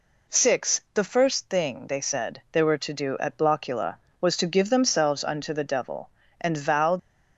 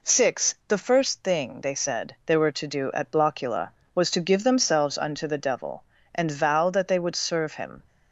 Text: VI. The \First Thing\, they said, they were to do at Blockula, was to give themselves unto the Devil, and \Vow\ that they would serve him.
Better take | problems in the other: second | stops before "that they would serve him"; at 6.9 s

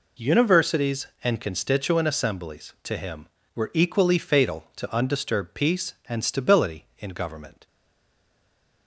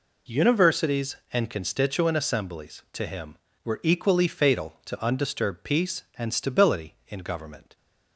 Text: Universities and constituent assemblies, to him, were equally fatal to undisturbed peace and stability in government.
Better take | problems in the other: second | stays silent after the last word; noticeable; from 7.6 s on; 1.2 s long

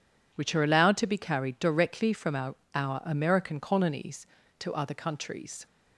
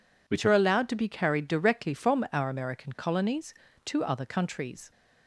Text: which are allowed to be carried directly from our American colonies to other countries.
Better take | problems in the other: second | says "our" twice; at 2.7 s

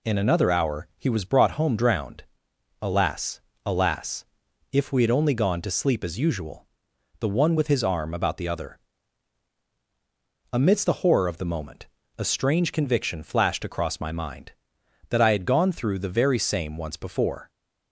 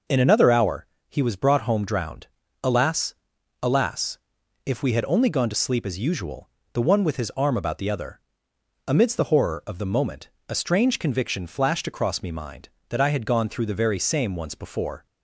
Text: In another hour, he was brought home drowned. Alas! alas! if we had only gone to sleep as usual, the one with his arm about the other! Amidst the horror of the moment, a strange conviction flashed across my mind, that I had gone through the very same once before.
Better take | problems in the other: first | says "me" for "my"; at 12.2 s

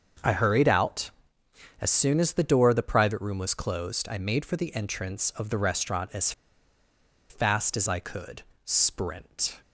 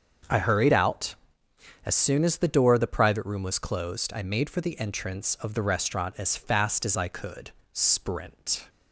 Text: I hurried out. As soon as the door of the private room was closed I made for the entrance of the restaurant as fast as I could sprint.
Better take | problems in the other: second | starts louder than the rest; until 1.9 s; 6.5 dB; also in the second // pauses between "as" and "fast"; at 6.3 s; 0.98 s long // pauses between "could" and "sprint"; slight; at 8.4 s; 0.24 s long; slight in the second

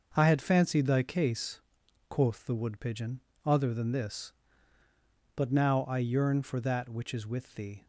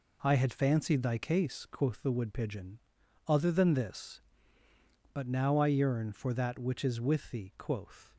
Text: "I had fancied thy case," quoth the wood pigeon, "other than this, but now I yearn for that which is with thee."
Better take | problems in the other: first | goes on to say "Quoth"; from 7.5 s on; 0.56 s long

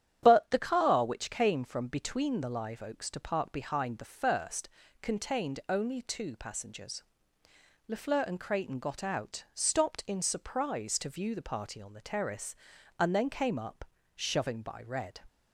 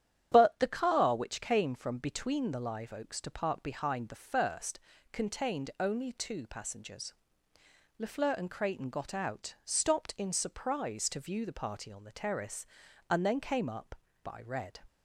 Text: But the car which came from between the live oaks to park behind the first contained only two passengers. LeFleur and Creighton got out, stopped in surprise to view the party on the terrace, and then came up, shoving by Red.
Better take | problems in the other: first | starts louder than the rest; strong; until 1.3 s; 10 dB; strong in the first // pauses between "first" and "contained"; slight; at 4.7 s; 0.34 s long; slight in the first // skips "shoving"; at 14.0 s

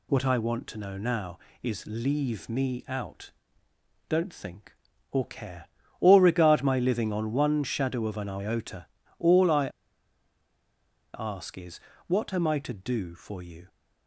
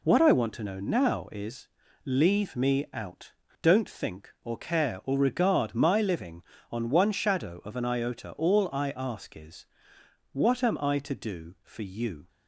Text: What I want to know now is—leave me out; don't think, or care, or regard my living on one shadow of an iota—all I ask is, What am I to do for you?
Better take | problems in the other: second | pauses between "I" and "ask"; strong; at 9.6 s; 1.4 s long

